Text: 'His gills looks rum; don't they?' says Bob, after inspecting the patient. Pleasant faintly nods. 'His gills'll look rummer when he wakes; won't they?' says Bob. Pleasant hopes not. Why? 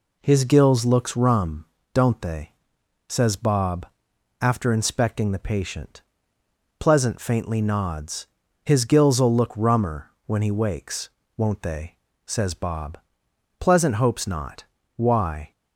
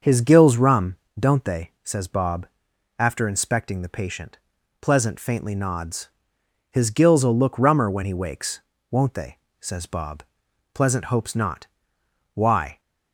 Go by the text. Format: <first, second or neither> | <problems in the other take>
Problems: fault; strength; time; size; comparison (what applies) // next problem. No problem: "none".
first | starts louder than the rest; until 1.2 s; 6.5 dB // skips "looks"; at 0.5 s